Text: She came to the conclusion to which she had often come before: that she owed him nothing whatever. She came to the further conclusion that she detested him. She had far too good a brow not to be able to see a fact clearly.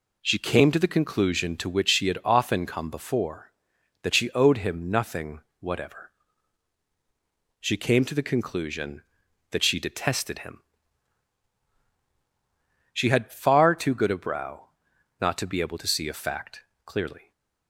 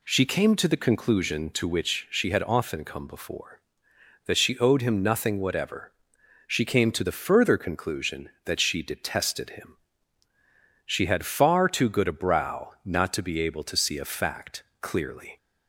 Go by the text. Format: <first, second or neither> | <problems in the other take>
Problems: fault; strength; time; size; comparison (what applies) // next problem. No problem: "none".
second | pauses between "nothing" and "whatever"; slight; at 5.4 s; 0.18 s long // skips "further"; at 8.2 s // pauses between "brow" and "not"; noticeable; at 14.6 s; 0.52 s long // pauses between "fact" and "clearly"; slight; at 16.6 s; 0.22 s long; slight in the second